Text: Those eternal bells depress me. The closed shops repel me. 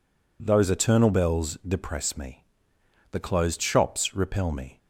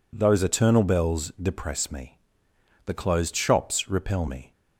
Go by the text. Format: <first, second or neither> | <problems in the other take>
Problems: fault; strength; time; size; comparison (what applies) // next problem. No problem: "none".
neither | none